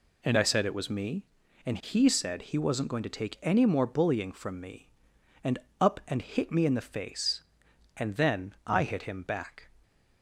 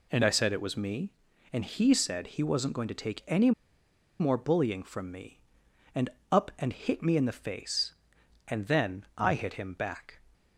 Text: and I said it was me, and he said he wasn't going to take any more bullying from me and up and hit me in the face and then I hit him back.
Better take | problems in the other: first | pauses between "any" and "more"; noticeable; at 3.5 s; 0.69 s long // pauses between "and" and "up"; slight; at 6.0 s; 0.22 s long; slight in the first

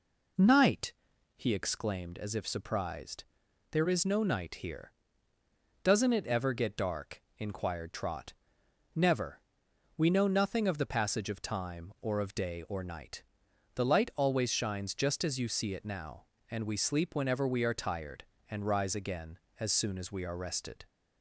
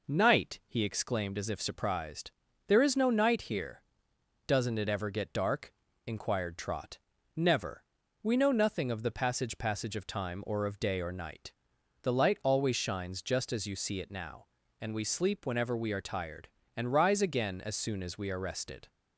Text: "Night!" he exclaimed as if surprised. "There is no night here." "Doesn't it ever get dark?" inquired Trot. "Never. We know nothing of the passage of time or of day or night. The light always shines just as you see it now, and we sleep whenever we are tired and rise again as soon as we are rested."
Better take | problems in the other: first | says "passage" twice; at 9.5 s

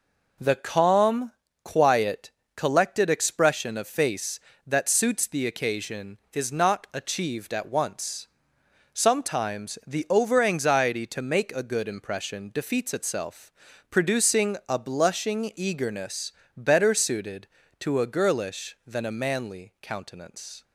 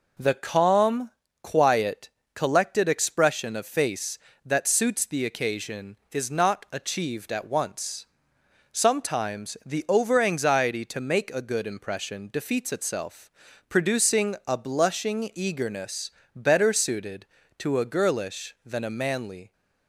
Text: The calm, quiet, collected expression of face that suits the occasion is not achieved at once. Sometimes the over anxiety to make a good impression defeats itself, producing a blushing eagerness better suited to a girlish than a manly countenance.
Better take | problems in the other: first | pauses between "eagerness" and "better"; slight; at 16.0 s; 0.24 s long; slight in the first // stops before "countenance"; at 19.5 s

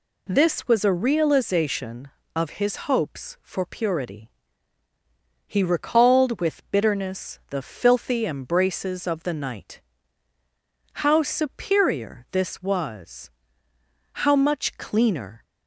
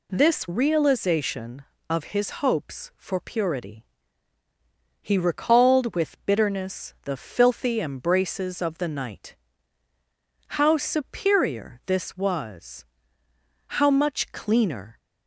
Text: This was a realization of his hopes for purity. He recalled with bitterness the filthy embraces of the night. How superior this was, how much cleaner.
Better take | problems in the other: first | skips "was a"; at 0.4 s

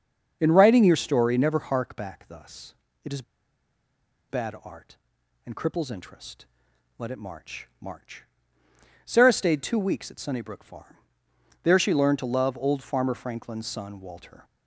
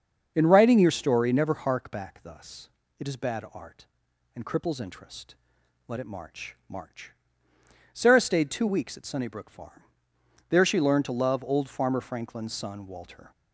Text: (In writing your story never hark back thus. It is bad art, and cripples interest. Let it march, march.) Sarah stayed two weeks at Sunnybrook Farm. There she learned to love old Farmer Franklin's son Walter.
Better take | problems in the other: second | starts louder than the rest; until 1.4 s; 6.5 dB; also in the second // pauses between "is" and "bad"; at 3.2 s; 1.0 s long

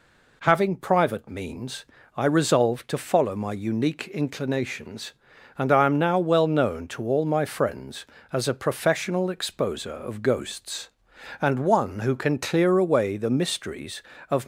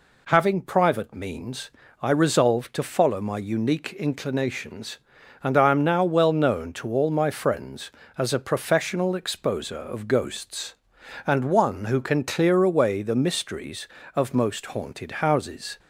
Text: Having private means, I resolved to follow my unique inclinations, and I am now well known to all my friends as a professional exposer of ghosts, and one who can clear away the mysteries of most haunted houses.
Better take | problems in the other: second | stops before "most haunted houses"; at 14.4 s

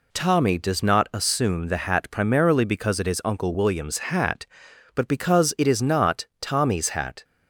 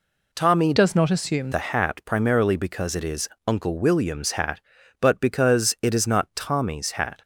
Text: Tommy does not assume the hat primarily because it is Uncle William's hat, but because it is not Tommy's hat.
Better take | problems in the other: first | changes voice from "does" to "assume"; from 0.7 to 1.5 s; 0.8 s long // pauses between "is" and "Uncle"; slight; at 3.2 s; 0.18 s long

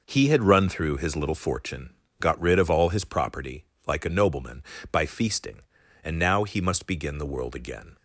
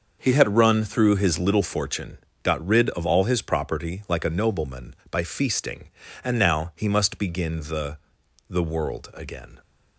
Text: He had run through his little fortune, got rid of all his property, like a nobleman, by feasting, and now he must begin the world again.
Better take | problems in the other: first | starts louder than the rest; noticeable; until 1.2 s; 6 dB // says "the" twice; at 8.4 s

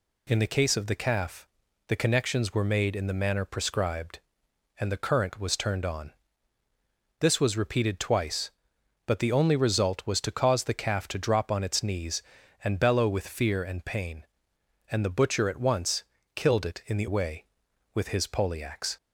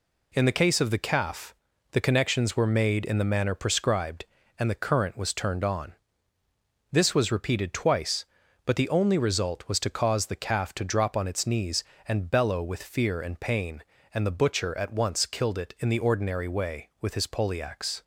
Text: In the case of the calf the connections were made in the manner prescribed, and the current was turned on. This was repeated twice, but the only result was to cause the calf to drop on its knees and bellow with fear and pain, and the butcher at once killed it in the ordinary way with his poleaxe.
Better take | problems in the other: second | pauses between "calf" and "the"; at 1.4 s; 0.38 s long; also in the second // pauses between "once" and "killed"; slight; at 16.0 s; 0.30 s long // skips "ordinary"; at 17.0 s

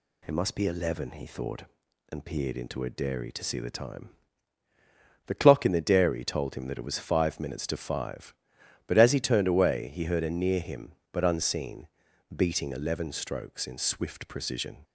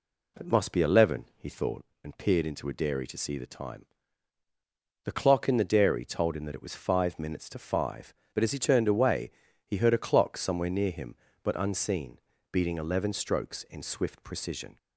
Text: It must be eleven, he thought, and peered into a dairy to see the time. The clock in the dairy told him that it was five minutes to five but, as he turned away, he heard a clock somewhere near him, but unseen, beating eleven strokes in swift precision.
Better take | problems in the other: second | skips "clock somewhere"; at 10.2 s

